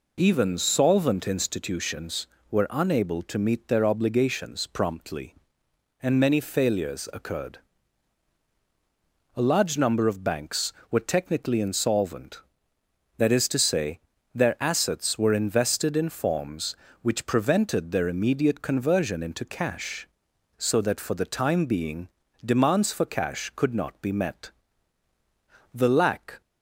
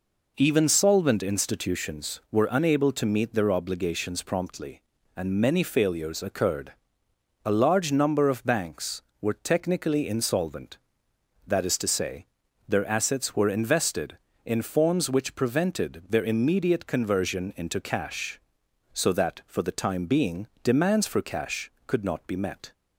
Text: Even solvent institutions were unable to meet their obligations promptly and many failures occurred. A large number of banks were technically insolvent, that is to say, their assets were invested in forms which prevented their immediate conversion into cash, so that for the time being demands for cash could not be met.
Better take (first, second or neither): second